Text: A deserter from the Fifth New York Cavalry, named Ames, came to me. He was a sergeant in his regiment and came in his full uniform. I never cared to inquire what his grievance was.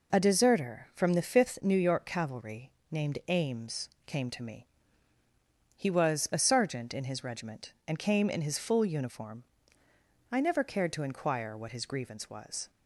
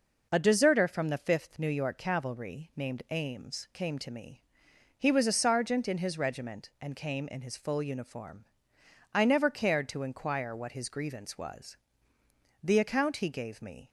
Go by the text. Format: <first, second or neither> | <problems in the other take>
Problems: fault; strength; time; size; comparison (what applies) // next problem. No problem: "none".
first | goes on to say "The account he gave me"; noticeable; from 12.6 s on; 1.2 s long